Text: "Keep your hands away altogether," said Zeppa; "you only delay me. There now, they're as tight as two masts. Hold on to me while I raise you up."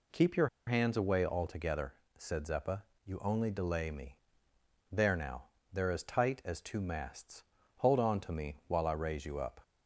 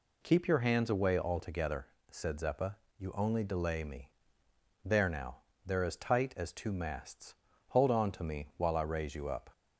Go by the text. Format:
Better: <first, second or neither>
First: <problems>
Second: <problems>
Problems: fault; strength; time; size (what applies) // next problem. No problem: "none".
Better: second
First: pauses between "your" and "hands"; slight; at 0.4 s; 0.19 s long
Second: none